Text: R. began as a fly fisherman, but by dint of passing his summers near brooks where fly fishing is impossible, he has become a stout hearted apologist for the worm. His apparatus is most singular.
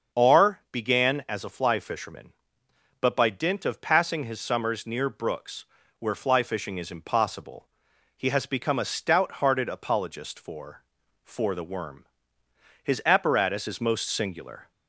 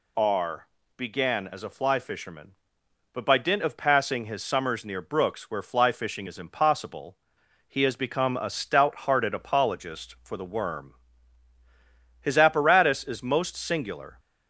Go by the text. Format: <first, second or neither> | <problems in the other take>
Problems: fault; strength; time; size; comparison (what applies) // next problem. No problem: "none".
second | starts louder than the rest; until 1.2 s; 6.5 dB // pauses between "brooks" and "where"; slight; at 5.6 s; 0.36 s long // says "for" twice; at 11.2 s